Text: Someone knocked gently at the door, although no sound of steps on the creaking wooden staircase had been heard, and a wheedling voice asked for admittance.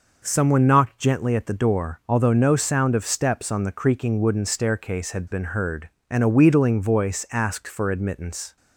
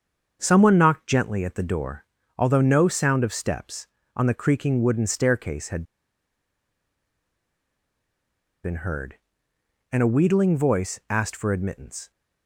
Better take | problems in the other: first | starts louder than the rest; until 1.4 s; 7 dB // pauses between "had" and "been"; strong; at 5.8 s; 2.7 s long

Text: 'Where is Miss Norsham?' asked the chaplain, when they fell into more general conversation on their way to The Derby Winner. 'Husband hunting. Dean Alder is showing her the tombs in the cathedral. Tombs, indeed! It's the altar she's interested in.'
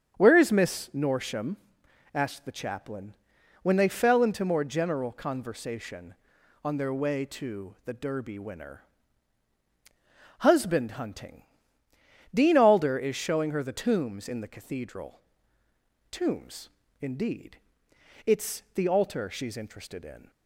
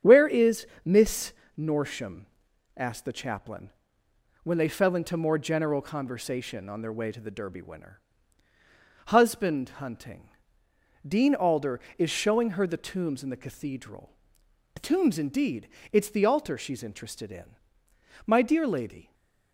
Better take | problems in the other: first | starts louder than the rest; strong; until 1.2 s; 8 dB; strong in the first // pauses between "is" and "Miss"; slight; at 0.6 s; 0.18 s long // pauses between "Miss" and "Norsham"; slight; at 1.3 s; 0.26 s long // goes on to say "My dear lady"; noticeable; from 18.2 s on; 0.88 s long // stays silent after the last word; slight; from 19.0 s on; 0.5 s long

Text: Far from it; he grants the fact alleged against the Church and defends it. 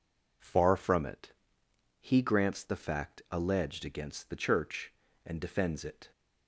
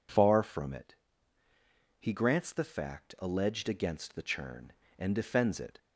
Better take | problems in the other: first | says "Churn" for "Church"; at 4.2 s

